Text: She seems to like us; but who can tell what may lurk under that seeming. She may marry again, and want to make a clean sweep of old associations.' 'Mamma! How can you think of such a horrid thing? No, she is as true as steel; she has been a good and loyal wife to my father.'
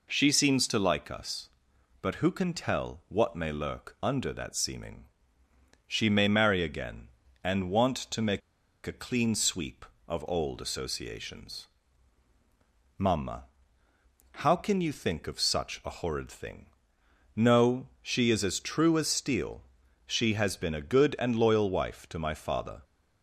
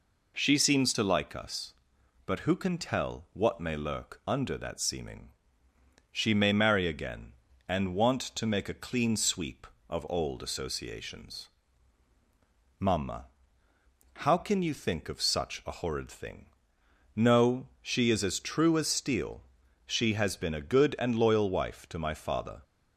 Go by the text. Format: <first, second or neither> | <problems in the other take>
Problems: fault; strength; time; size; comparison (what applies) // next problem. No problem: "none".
second | pauses between "make" and "a"; at 8.4 s; 0.45 s long